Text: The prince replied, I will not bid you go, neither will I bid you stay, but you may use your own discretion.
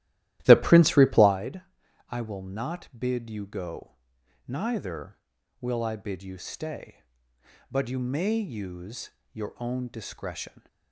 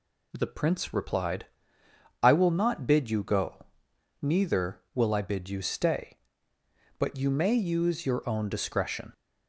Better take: second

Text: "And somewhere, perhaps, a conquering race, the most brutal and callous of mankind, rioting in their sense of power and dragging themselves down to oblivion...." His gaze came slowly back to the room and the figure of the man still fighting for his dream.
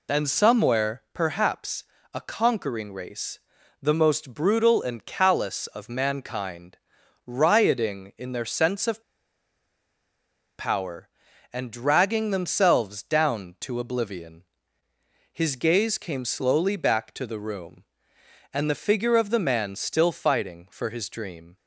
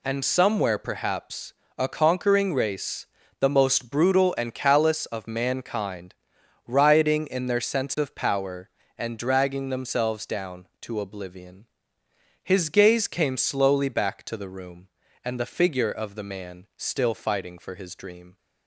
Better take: second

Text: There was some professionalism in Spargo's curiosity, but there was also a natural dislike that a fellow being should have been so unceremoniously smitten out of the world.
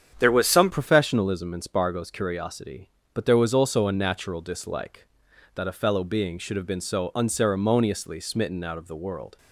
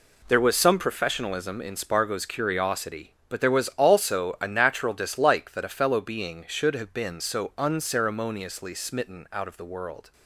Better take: second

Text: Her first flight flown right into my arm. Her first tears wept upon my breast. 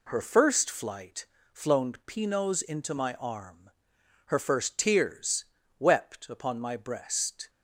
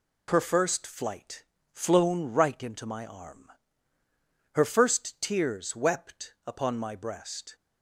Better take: second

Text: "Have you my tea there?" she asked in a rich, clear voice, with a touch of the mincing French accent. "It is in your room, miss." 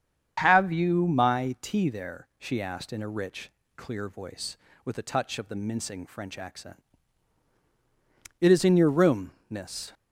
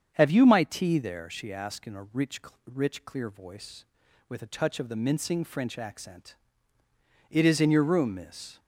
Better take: first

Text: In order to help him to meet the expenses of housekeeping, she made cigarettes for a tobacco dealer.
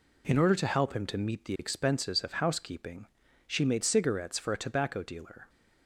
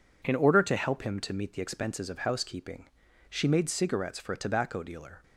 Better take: neither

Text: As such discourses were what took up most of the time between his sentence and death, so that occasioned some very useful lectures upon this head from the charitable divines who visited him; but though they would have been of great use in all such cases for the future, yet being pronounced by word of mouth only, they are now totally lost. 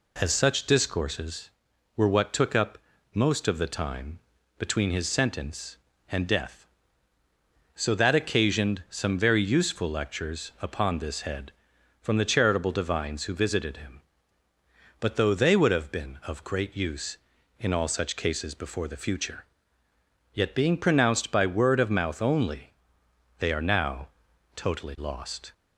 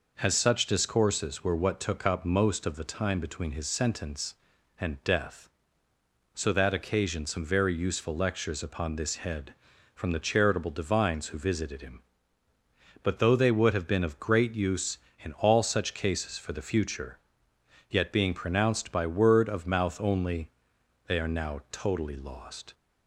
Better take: second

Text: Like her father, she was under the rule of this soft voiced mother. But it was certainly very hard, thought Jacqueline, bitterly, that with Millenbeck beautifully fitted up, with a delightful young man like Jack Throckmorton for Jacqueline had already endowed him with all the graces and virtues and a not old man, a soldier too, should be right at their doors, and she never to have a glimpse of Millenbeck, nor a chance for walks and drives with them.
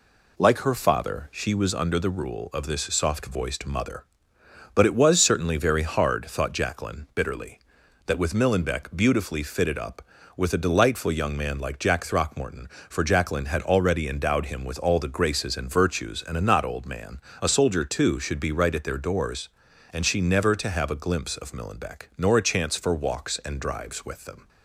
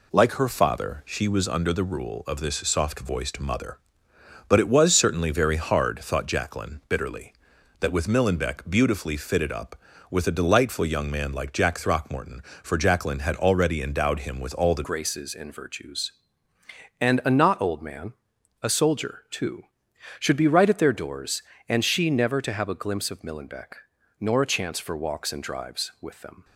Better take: first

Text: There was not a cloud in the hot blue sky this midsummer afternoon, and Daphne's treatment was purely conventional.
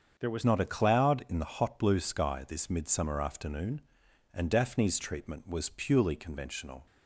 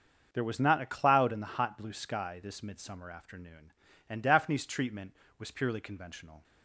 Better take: second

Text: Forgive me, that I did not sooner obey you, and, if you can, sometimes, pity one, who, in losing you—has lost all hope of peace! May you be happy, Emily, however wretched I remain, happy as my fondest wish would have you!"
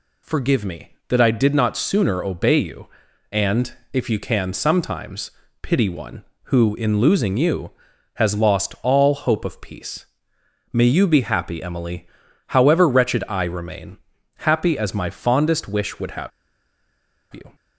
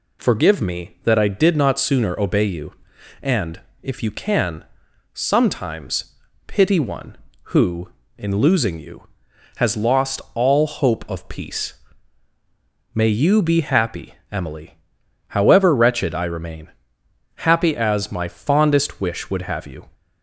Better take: second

